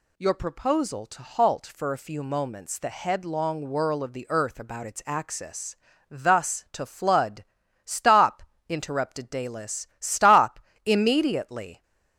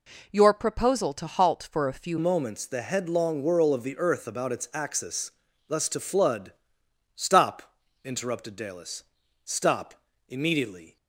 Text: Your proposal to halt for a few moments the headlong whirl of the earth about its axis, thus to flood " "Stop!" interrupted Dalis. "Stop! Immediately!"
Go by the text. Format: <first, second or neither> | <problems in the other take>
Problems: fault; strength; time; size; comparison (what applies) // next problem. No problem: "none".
first | changes voice at "moments"; from 2.1 s on; 8.8 s long